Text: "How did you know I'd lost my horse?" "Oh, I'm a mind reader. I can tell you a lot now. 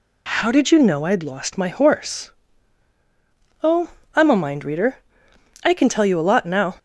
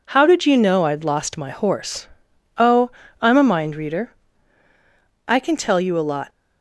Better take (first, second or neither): first